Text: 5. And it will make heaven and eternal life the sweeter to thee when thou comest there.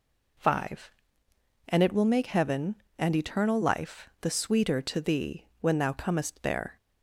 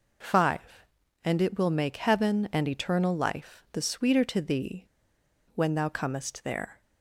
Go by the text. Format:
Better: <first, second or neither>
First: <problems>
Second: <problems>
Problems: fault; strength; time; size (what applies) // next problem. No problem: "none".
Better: first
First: none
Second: pauses between "thee" and "when"; noticeable; at 4.8 s; 0.69 s long